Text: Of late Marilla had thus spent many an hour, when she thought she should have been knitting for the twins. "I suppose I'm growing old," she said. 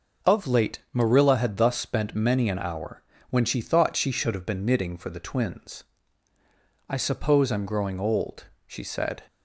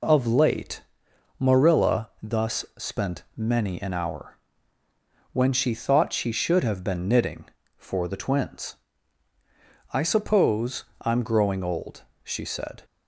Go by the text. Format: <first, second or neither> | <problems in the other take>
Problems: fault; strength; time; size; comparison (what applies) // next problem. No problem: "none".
first | pauses between "late" and "Marilla"; noticeable; at 0.8 s; 0.58 s long // skips "had"; at 2.1 s // pauses between "suppose" and "I'm"; slight; at 10.8 s; 0.16 s long